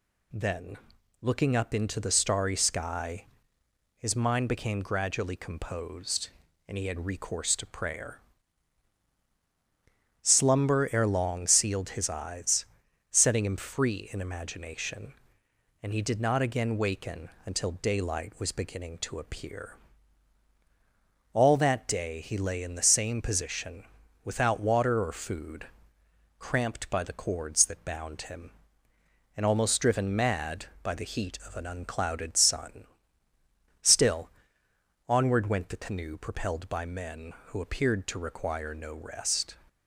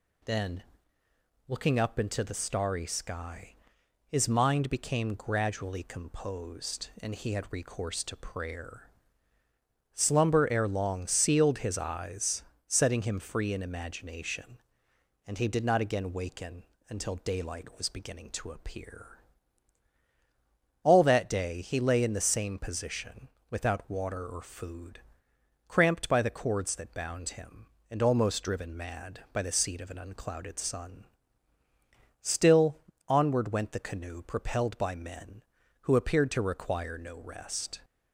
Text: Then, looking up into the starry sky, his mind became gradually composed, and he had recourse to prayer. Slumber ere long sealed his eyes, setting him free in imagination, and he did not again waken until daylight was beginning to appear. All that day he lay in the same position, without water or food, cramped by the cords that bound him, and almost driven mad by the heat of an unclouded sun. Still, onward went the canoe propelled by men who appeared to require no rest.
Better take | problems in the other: first | pauses between "waken" and "until"; slight; at 16.6 s; 0.24 s long; slight in the first // says "seat" for "heat"; at 29.5 s

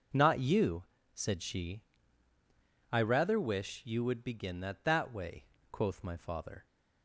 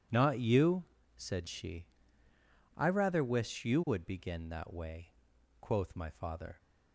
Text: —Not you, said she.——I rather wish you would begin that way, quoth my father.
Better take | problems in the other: second | says "that" twice; at 4.8 s

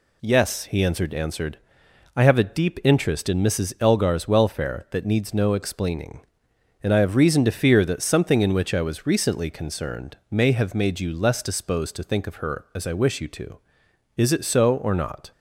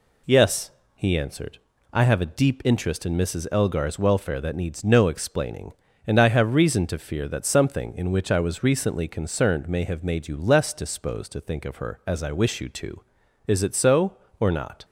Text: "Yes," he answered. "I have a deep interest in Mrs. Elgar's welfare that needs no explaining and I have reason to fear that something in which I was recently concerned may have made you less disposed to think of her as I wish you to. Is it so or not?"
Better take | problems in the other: second | says "answered" twice; at 1.1 s // pauses between "concerned" and "may"; slight; at 10.1 s; 0.16 s long

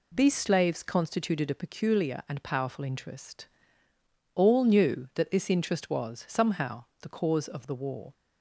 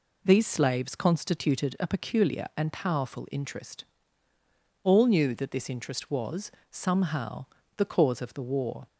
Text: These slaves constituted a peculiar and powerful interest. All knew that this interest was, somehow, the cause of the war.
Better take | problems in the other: neither | none

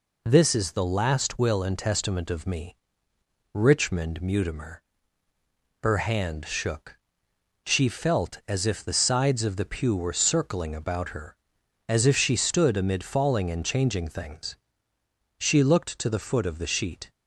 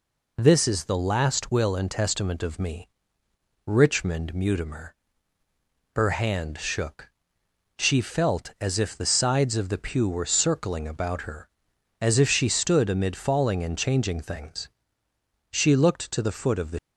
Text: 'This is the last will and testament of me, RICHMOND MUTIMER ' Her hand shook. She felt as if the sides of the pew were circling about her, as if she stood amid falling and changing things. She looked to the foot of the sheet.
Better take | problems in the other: first | stops before "sheet"; at 16.7 s

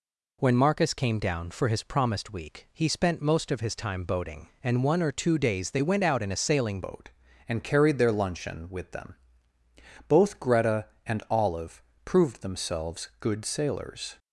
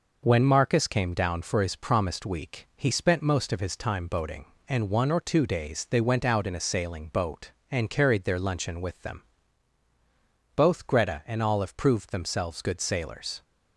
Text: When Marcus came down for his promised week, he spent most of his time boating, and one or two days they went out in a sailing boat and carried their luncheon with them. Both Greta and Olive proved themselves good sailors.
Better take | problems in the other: second | changes voice at "boat"; from 6.8 s on; 7.3 s long // pauses between "Olive" and "proved"; slight; at 11.8 s; 0.24 s long

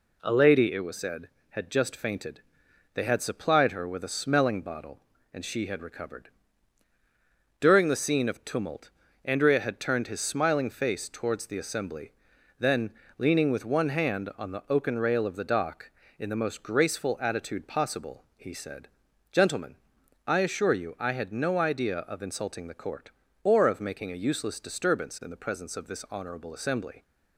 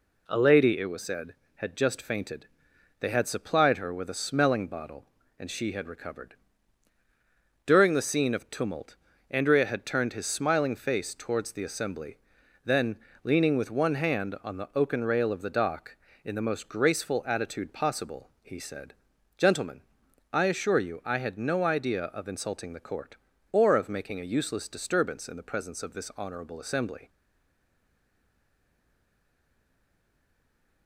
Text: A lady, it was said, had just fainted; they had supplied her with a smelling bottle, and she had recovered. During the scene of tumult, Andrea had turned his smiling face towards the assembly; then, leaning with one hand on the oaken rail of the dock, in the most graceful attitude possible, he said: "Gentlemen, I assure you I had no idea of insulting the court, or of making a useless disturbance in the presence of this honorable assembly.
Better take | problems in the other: first | stays silent after the last word; strong; from 27.0 s on; 3.8 s long

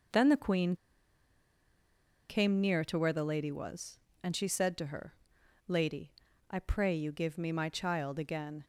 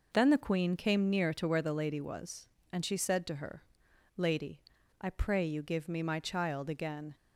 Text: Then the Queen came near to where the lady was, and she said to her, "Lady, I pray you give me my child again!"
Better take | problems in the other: second | pauses between "Queen" and "came"; strong; at 0.7 s; 1.5 s long

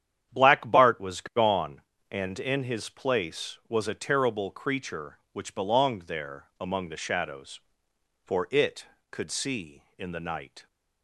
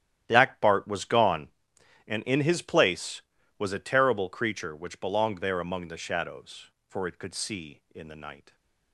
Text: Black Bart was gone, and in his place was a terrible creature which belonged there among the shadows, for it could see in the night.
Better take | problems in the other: first | gets quieter; strong; throughout; 15 dB // starts louder than the rest; strong; until 1.2 s; 11 dB; strong in the first

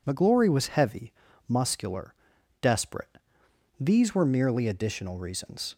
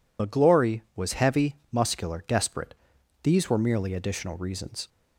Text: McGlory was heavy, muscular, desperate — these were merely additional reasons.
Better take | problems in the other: first | loses the start of "McGlory"; at 0.1 s; 75 ms

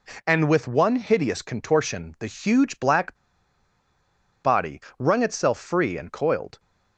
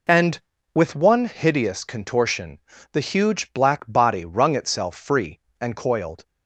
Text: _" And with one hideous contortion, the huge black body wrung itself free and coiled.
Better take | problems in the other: second | pauses between "black" and "body"; strong; at 3.1 s; 1.2 s long // pauses between "body" and "wrung"; slight; at 4.7 s; 0.20 s long

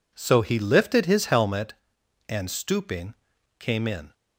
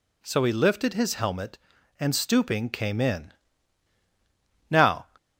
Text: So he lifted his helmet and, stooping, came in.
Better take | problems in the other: first | goes on to say "Now"; slight; from 4.6 s on; 0.38 s long

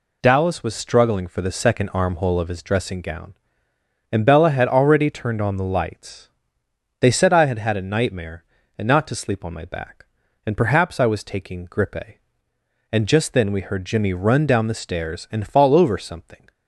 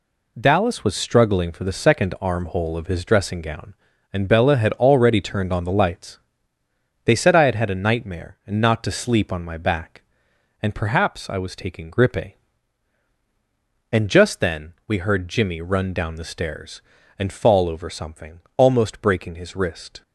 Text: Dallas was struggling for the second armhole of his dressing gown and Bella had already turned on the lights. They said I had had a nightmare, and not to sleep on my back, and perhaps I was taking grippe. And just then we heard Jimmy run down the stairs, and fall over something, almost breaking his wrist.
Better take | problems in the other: second | stops before "almost breaking his wrist"; at 16.5 s

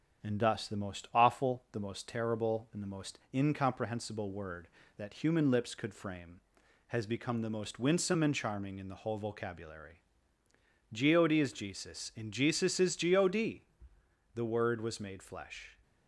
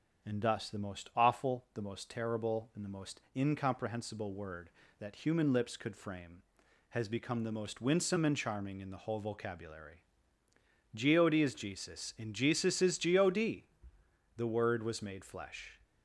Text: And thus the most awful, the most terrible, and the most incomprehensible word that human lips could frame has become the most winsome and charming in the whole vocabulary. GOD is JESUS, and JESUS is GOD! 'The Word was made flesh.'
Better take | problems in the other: second | gets quieter; throughout; 6.5 dB // starts louder than the rest; strong; until 1.3 s; 8 dB; strong in the second

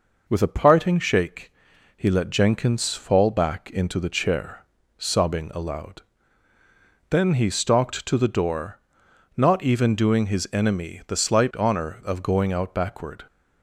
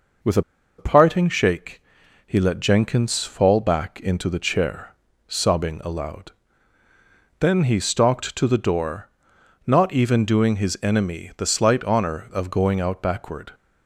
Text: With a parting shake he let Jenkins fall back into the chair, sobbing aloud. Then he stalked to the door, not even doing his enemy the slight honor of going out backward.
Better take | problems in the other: first | pauses between "a" and "parting"; at 0.4 s; 0.36 s long // pauses between "shake" and "he"; at 1.8 s; 0.44 s long; also in the first

